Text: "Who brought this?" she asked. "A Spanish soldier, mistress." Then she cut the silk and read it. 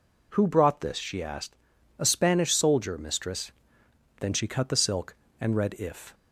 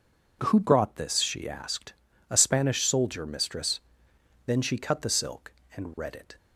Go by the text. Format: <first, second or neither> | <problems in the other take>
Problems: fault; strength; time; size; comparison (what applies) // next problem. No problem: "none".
second | says "if" for "it"; at 5.7 s